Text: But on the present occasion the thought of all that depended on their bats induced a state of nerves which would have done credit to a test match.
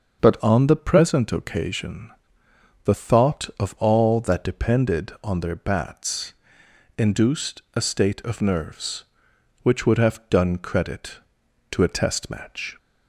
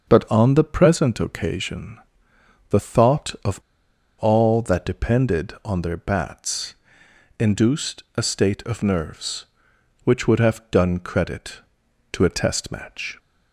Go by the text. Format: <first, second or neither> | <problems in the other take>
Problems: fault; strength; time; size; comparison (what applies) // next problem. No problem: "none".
first | starts louder than the rest; until 1.1 s; 6.5 dB; also in the first // pauses between "occasion" and "the"; noticeable; at 1.9 s; 0.72 s long; noticeable in the first // pauses between "of" and "all"; noticeable; at 3.6 s; 0.59 s long // pauses between "bats" and "induced"; noticeable; at 6.7 s; 0.66 s long; noticeable in the first